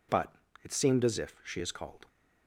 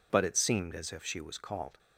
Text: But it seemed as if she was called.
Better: second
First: pauses between "But" and "it"; slight; at 0.3 s; 0.32 s long // says "is" for "was"; at 1.5 s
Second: none

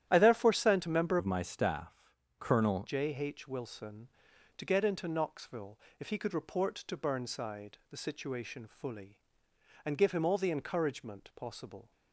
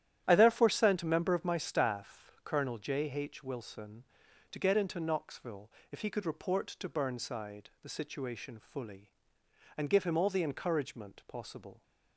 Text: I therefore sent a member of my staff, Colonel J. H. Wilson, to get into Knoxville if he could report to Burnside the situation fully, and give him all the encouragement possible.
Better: second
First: starts louder than the rest; strong; until 1.1 s; 11.5 dB // changes voice from "of" to "Colonel"; from 1.1 to 2.8 s; 1.7 s long // pauses between "Knoxville" and "if"; slight; at 5.7 s; 0.22 s long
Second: starts louder than the rest; strong; until 1.2 s; 11 dB // pauses between "Knoxville" and "if"; slight; at 5.7 s; 0.22 s long

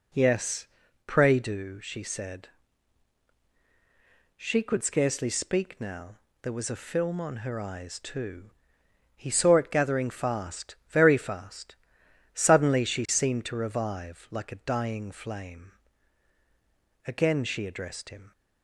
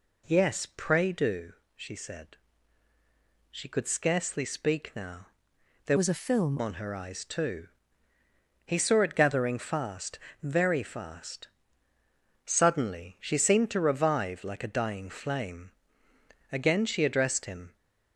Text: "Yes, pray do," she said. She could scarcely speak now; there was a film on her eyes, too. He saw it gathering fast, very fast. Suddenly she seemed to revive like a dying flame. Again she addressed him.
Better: first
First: none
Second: changes voice from "was" to "film"; from 5.9 to 6.5 s; 0.6 s long

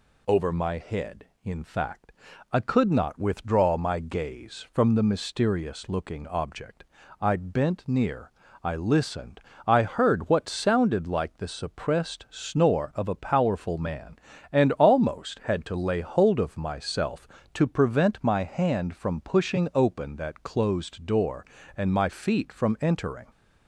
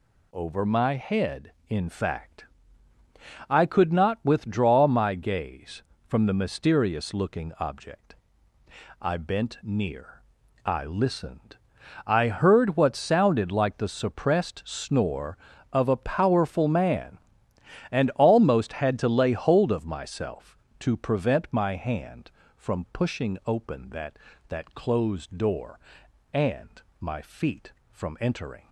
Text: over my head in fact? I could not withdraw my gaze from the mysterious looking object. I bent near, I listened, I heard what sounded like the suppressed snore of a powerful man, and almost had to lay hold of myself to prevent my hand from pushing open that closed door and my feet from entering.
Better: first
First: none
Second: says "that" twice; at 24.4 s // pauses between "and" and "my"; slight; at 26.8 s; 0.18 s long

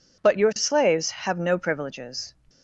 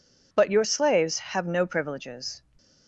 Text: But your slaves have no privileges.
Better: neither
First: none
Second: none

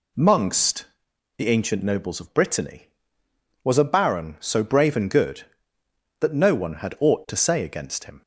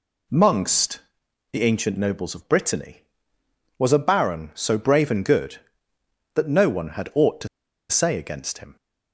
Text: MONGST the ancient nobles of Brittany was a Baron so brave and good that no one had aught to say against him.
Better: first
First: pauses between "MONGST" and "the"; noticeable; at 0.8 s; 0.54 s long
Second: pauses between "MONGST" and "the"; noticeable; at 0.9 s; 0.54 s long // pauses between "to" and "say"; at 7.4 s; 0.42 s long

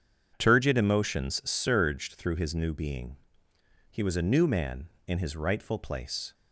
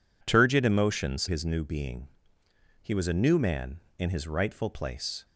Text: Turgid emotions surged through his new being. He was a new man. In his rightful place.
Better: first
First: none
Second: skips "surged through"; at 1.2 s

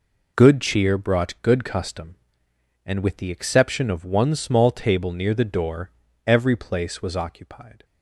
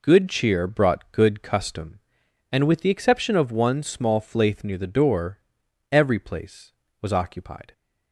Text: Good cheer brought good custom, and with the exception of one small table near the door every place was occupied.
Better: first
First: pauses between "door" and "every"; slight; at 5.9 s; 0.36 s long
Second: says "flaith" for "table"; at 4.2 s // pauses between "door" and "every"; noticeable; at 5.3 s; 0.52 s long

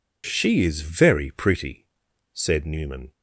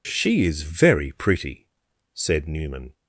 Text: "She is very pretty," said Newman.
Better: neither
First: none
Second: none

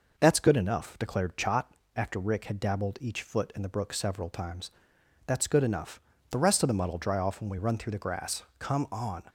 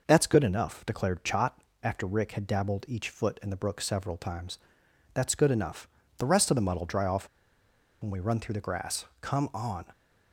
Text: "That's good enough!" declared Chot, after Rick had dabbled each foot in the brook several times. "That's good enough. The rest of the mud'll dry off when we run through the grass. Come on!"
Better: first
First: none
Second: pauses between "off" and "when"; noticeable; at 7.2 s; 0.75 s long

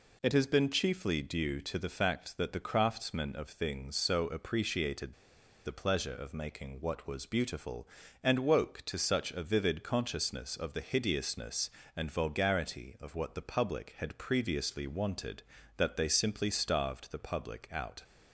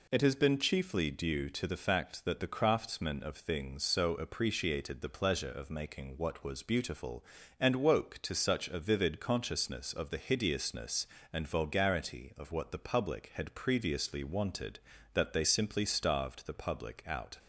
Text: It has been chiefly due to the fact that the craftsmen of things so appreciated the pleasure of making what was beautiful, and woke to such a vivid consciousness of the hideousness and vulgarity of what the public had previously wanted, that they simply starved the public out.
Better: second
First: pauses between "appreciated" and "the"; noticeable; at 5.1 s; 0.52 s long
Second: none

